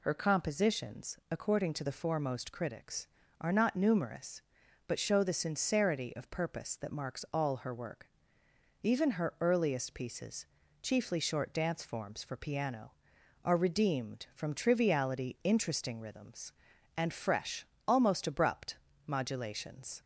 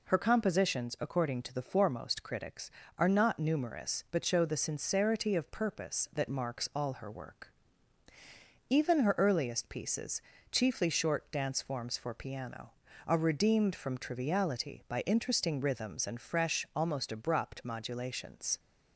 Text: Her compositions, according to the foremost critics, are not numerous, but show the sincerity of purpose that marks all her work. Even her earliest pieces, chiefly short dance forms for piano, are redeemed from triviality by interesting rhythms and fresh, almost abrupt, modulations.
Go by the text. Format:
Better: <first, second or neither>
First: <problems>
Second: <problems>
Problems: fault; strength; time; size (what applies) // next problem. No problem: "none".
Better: second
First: skips "by"; at 15.4 s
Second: none